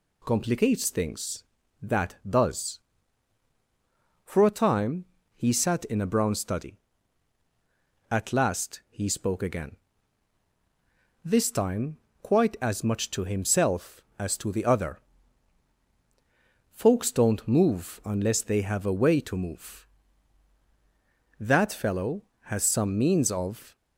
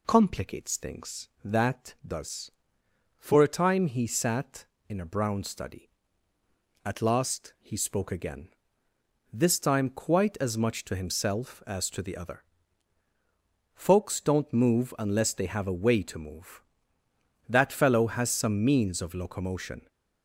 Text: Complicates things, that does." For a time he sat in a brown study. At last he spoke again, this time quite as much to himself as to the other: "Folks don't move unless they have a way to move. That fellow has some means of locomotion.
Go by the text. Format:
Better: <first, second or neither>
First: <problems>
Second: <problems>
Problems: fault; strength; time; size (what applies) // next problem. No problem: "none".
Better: second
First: pauses between "time" and "he"; slight; at 5.0 s; 0.30 s long // pauses between "time" and "quite"; slight; at 11.9 s; 0.24 s long // stops before "locomotion"; at 23.7 s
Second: none